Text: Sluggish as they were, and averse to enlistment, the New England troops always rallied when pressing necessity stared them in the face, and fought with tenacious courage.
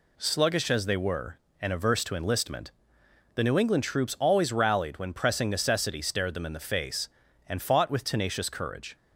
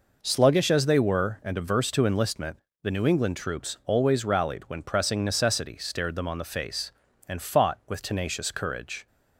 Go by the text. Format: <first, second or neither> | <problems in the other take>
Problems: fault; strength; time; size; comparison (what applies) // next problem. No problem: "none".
first | says "on" for "in"; at 6.2 s